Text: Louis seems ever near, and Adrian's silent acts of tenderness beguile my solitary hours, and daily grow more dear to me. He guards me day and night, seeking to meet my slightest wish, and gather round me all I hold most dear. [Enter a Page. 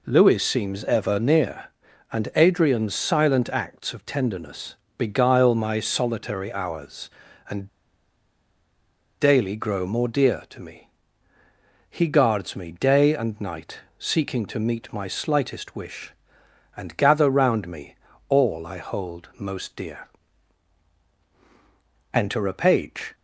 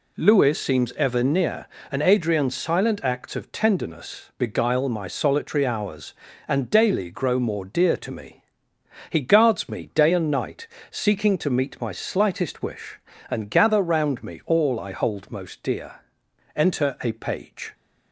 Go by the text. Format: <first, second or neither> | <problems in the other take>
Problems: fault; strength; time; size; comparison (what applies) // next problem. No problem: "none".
second | pauses between "tenderness" and "beguile"; slight; at 4.7 s; 0.24 s long // pauses between "and" and "daily"; strong; at 7.6 s; 1.5 s long // pauses between "me" and "all"; slight; at 17.9 s; 0.34 s long